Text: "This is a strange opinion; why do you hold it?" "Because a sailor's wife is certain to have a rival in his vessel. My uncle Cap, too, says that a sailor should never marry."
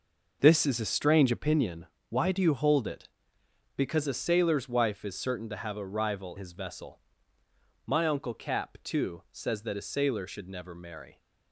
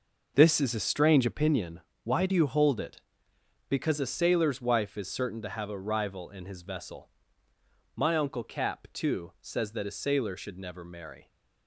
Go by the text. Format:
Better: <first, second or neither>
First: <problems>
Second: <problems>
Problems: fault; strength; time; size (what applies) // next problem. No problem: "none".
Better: second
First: skips "in"; at 6.3 s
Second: none